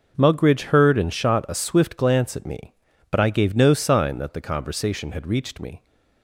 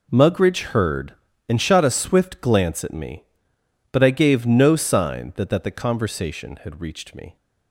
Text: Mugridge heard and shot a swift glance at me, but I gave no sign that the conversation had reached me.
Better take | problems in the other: first | says "that" twice; at 5.4 s

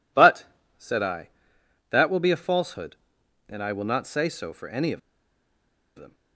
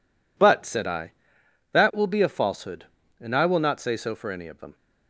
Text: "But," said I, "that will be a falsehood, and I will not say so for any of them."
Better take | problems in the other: second | pauses between "of" and "them"; noticeable; at 4.9 s; 0.96 s long

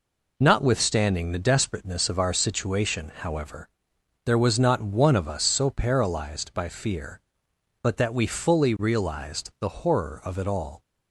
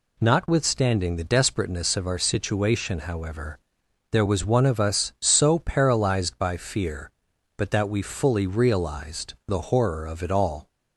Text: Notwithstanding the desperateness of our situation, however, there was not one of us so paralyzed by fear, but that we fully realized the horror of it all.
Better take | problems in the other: first | skips "not"; at 4.4 s

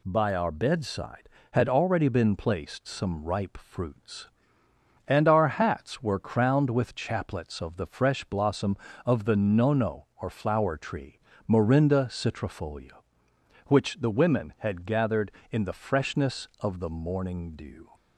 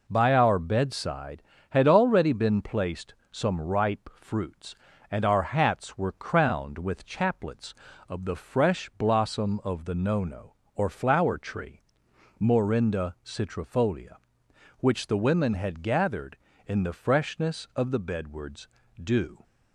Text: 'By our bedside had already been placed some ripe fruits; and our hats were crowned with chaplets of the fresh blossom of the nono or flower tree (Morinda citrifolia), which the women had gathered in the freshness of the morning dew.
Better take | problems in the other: first | pauses between "placed" and "some"; slight; at 3.1 s; 0.16 s long // says "bedwards" for "morning"; at 17.9 s

